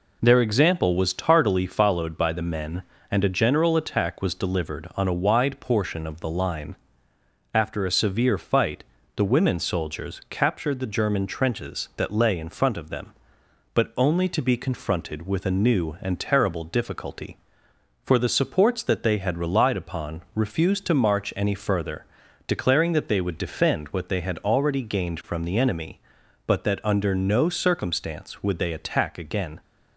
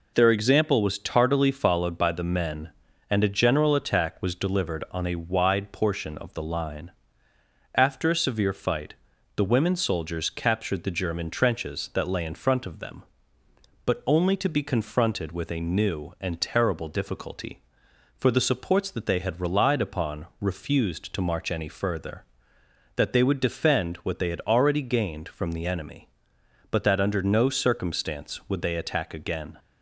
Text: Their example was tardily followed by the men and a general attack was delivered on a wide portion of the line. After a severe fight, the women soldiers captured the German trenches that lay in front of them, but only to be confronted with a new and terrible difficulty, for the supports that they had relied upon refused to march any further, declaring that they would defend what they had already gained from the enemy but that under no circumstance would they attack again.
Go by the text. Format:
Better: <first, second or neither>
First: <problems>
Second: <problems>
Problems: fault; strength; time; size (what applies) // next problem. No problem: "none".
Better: first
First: none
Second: skips "declaring"; at 22.5 s